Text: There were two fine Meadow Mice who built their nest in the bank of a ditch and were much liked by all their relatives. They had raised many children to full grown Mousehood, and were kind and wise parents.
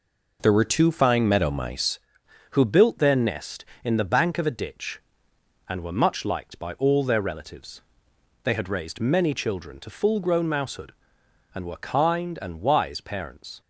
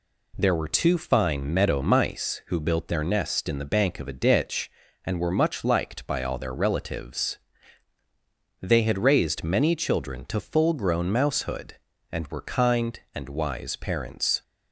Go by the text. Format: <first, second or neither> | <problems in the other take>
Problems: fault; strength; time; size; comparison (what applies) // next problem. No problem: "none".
second | changes voice at "who"; from 2.5 s on; 11.0 s long